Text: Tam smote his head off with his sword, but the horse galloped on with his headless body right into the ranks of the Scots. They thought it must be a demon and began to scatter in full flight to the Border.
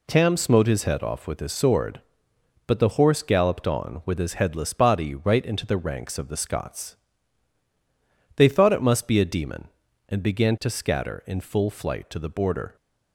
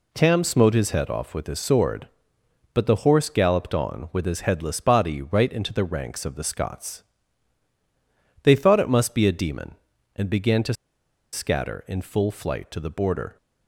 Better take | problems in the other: first | pauses between "to" and "scatter"; noticeable; at 10.7 s; 0.59 s long

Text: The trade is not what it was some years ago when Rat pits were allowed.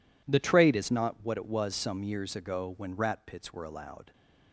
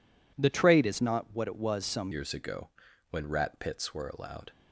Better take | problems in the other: first | changes voice at "years"; from 2.1 s on; 2.4 s long // pauses between "ago" and "when"; at 2.6 s; 0.42 s long

